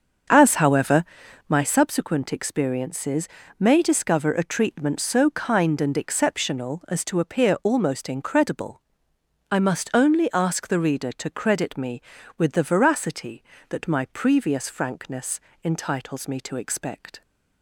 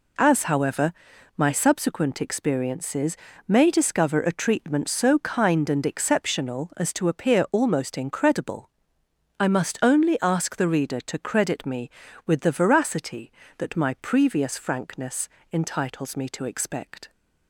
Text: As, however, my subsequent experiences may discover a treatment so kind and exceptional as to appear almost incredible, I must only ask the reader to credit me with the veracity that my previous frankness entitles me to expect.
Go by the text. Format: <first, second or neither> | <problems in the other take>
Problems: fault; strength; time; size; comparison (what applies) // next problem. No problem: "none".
second | starts louder than the rest; until 1.6 s; 7 dB // pauses between "experiences" and "may"; slight; at 3.2 s; 0.32 s long; slight in the second // pauses between "frankness" and "entitles"; slight; at 15.3 s; 0.24 s long; slight in the second